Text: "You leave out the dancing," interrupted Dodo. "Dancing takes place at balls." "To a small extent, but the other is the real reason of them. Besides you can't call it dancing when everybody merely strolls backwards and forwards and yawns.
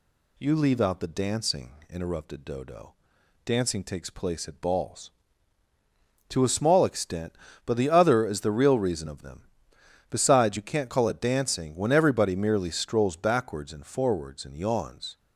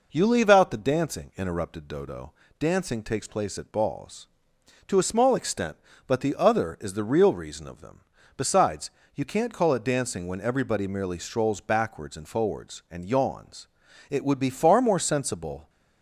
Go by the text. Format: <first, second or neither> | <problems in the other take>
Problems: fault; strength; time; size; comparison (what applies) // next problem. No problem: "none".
first | pauses between "Besides" and "you"; slight; at 8.8 s; 0.24 s long // goes on to say "It would be far more sensible"; from 14.0 s on; 1.6 s long